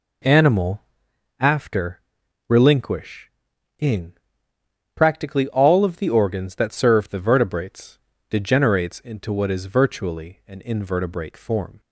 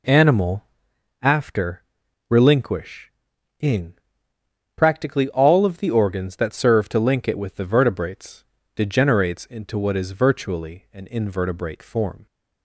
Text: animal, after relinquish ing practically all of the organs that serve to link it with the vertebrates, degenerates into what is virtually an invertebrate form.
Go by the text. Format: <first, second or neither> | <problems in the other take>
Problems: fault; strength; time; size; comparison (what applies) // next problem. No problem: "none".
second | pauses between "after" and "relinquish"; noticeable; at 1.9 s; 0.48 s long; noticeable in the second // pauses between "relinquish" and "ing"; noticeable; at 3.2 s; 0.50 s long; noticeable in the second // pauses between "ing" and "practically"; noticeable; at 4.1 s; 0.82 s long; noticeable in the second // skips "to link it with"; at 7.0 s